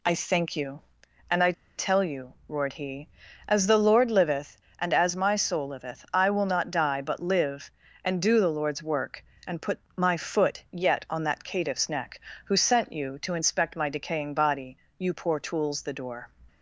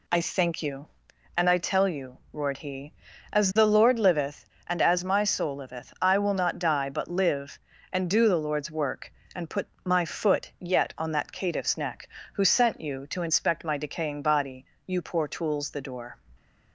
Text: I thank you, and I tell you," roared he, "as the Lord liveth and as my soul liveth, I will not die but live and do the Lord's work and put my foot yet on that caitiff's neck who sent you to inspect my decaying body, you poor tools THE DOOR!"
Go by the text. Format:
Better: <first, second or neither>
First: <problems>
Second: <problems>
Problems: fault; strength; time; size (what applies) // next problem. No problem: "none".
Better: second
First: pauses between "I" and "tell"; slight; at 1.5 s; 0.24 s long // pauses between "put" and "my"; slight; at 9.7 s; 0.16 s long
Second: pauses between "put" and "my"; slight; at 9.6 s; 0.16 s long